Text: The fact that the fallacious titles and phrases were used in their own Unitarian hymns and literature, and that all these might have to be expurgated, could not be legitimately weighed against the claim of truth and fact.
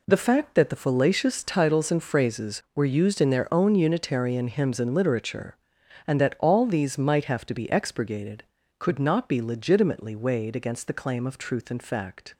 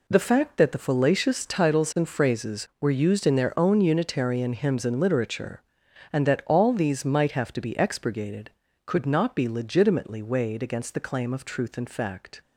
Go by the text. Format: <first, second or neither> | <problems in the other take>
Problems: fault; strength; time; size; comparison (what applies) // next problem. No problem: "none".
neither | none